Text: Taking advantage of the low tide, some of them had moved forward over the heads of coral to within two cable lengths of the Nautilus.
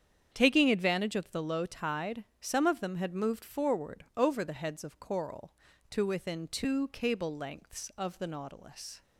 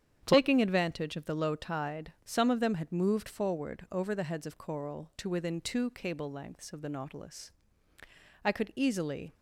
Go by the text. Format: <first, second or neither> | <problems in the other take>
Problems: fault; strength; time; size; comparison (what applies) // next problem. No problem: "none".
first | starts louder than the rest; strong; until 1.2 s; 9 dB; strong in the first // goes on to say "I could easily"; noticeable; from 8.4 s on; 0.92 s long